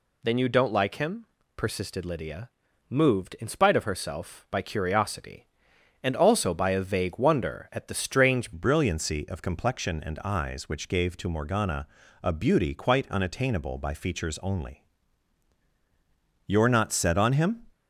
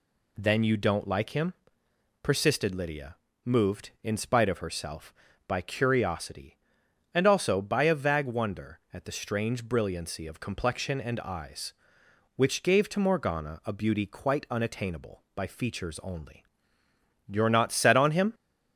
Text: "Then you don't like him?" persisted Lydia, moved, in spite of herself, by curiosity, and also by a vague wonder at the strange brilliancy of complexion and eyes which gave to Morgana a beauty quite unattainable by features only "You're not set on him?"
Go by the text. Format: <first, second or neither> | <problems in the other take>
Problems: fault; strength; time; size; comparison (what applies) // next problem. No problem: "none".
second | changes voice at "brilliancy"; from 8.5 s on; 9.1 s long // pauses between "Morgana" and "a"; slight; at 11.8 s; 0.34 s long // pauses between "only" and "You're"; strong; at 14.8 s; 1.6 s long; noticeable in the second